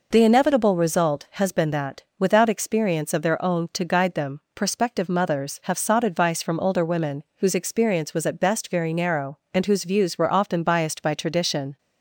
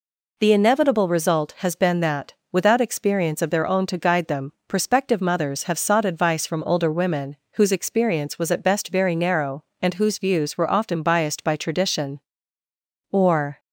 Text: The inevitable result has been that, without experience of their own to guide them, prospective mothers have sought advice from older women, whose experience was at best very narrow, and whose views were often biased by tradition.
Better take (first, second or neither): first